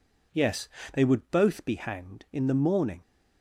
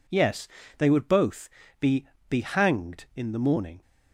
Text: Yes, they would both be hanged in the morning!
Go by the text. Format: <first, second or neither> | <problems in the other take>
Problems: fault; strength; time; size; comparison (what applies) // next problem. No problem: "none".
first | pauses between "both" and "be"; slight; at 1.4 s; 0.32 s long // says "be" twice; at 2.2 s